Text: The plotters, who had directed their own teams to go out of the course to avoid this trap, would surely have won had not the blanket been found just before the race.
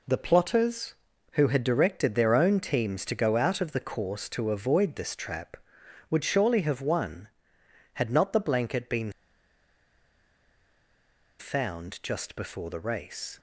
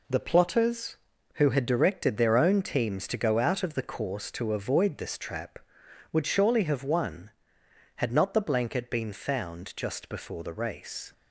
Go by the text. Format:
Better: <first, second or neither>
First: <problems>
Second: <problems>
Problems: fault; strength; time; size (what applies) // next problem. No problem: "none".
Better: second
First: pauses between "been" and "found"; strong; at 9.1 s; 2.2 s long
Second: none